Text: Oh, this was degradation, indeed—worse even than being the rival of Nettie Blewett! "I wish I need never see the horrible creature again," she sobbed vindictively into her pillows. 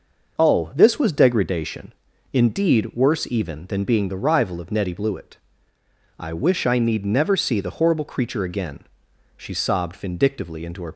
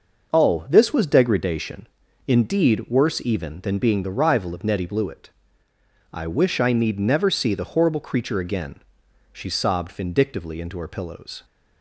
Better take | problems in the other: second | starts louder than the rest; noticeable; until 1.4 s; 6 dB; noticeable in the second // stops before "pillows"; at 10.9 s

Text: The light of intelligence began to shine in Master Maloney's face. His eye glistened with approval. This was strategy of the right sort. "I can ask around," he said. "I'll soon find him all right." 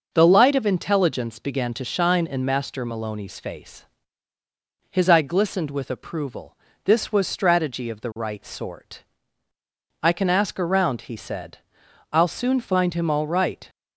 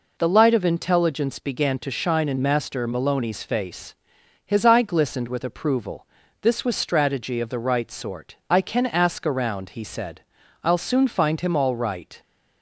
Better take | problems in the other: neither | none

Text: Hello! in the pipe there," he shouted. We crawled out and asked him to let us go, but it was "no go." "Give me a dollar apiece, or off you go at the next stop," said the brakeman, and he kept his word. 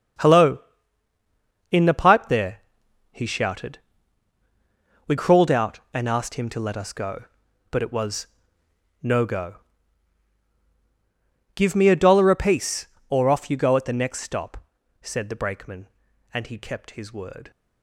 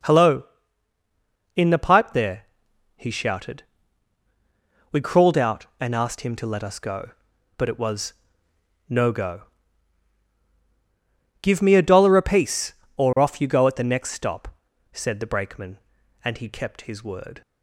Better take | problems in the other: second | gets quieter; strong; throughout; 10.5 dB // pauses between "was" and "no"; noticeable; at 8.2 s; 0.78 s long; noticeable in the second

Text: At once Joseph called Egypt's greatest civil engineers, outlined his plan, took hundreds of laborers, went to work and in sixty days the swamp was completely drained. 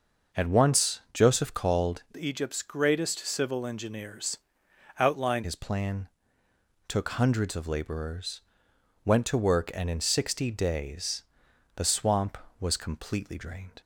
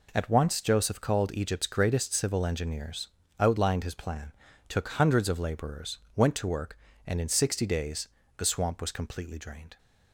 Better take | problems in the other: second | changes voice from "Egypt's" to "outlined"; from 2.1 to 5.4 s; 3.3 s long // pauses between "days" and "the"; noticeable; at 11.2 s; 0.54 s long; slight in the second

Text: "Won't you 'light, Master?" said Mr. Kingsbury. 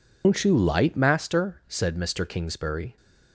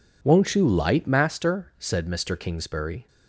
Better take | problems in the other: second | loses the start of "Won't"; at 0.2 s; 125 ms

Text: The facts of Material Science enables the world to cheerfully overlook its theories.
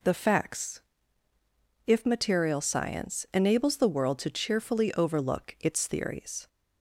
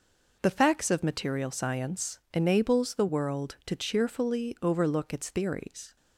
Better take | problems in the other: second | says "if" for "of"; at 1.8 s

